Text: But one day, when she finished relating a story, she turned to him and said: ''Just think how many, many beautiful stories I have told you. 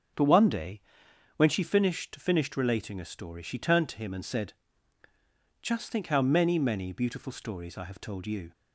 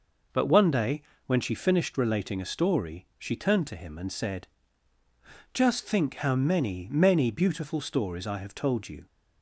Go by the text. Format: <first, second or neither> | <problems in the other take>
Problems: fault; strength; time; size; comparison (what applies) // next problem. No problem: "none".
second | starts louder than the rest; until 1.7 s; 6.5 dB // says "finished" twice; at 2.1 s